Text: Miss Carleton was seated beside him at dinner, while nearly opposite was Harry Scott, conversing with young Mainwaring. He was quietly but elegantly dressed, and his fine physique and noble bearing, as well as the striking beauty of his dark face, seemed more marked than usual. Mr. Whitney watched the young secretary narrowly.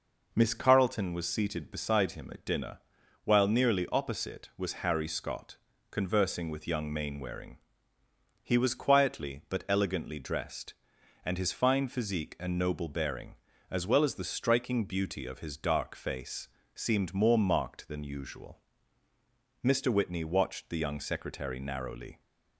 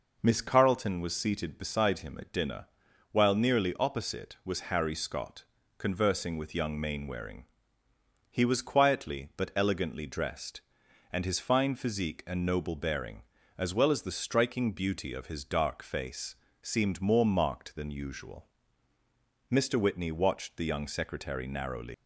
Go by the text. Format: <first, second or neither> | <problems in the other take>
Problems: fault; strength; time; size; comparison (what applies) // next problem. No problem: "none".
first | leaves "narrowly" unfinished; at 21.9 s; 140 ms